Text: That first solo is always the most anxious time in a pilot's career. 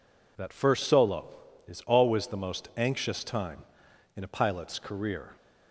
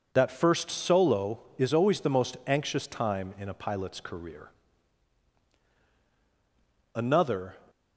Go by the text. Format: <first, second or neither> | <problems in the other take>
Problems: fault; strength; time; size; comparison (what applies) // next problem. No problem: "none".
first | goes on to say "Another"; noticeable; from 6.9 s on; 0.62 s long